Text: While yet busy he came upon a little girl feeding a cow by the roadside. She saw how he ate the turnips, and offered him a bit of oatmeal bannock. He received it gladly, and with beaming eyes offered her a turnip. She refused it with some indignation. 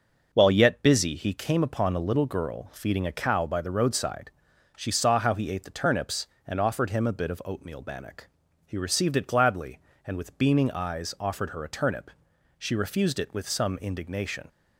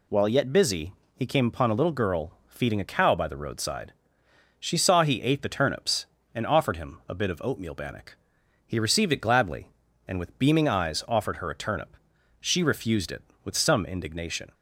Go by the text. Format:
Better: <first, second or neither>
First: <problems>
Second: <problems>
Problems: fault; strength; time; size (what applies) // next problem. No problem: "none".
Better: first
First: none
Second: pauses between "busy" and "he"; slight; at 0.9 s; 0.22 s long // skips "how"; at 5.0 s